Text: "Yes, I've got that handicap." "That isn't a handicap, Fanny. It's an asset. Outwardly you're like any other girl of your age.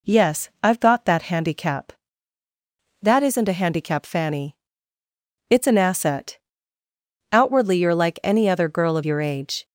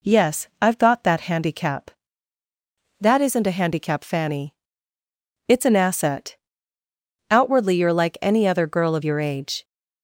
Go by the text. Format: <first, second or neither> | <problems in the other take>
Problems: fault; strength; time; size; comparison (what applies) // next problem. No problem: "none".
neither | none